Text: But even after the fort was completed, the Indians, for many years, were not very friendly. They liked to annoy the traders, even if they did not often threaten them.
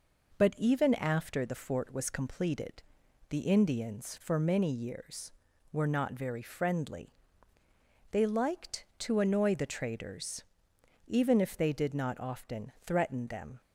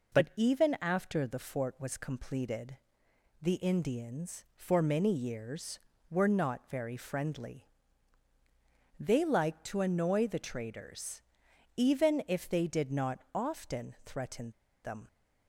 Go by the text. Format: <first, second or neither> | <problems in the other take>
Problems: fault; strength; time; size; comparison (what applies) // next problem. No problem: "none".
first | pauses between "threaten" and "them"; slight; at 14.5 s; 0.32 s long